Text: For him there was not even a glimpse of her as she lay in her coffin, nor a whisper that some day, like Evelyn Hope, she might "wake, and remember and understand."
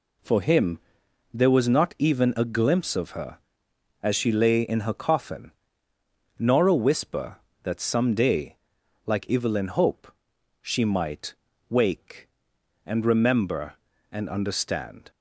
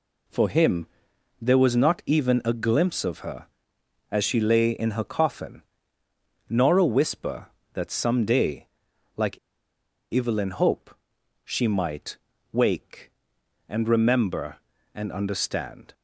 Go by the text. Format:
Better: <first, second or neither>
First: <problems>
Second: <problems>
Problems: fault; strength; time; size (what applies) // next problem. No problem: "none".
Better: first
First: pauses between "him" and "there"; noticeable; at 0.7 s; 0.54 s long // pauses between "might" and "wake"; slight; at 11.3 s; 0.36 s long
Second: pauses between "him" and "there"; noticeable; at 0.8 s; 0.54 s long // pauses between "like" and "Evelyn"; noticeable; at 9.3 s; 0.74 s long // pauses between "might" and "wake"; slight; at 12.1 s; 0.36 s long